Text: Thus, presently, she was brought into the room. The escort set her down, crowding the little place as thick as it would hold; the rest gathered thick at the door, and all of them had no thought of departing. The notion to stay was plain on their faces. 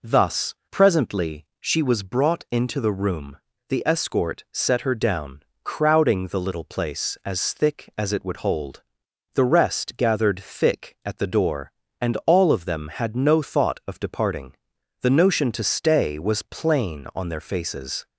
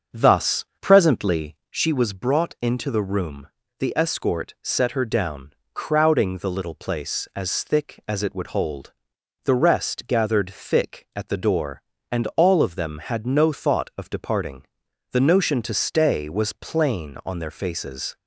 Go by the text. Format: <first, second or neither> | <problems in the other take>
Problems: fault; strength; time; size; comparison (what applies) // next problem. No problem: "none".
first | starts louder than the rest; until 1.8 s; 6.5 dB